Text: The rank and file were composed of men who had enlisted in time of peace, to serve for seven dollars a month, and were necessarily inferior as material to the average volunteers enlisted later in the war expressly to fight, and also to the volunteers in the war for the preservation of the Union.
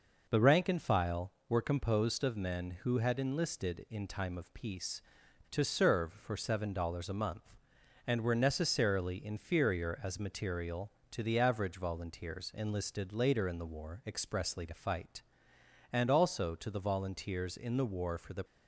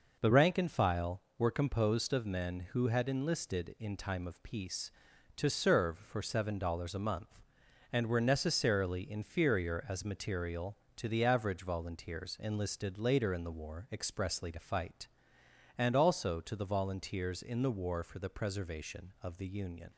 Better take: second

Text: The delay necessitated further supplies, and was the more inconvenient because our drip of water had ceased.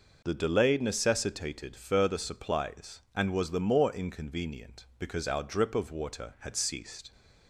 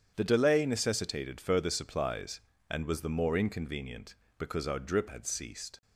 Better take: first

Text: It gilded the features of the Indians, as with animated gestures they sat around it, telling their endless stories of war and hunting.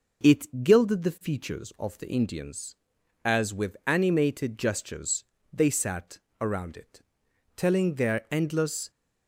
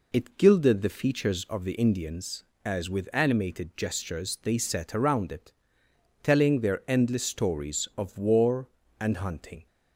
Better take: second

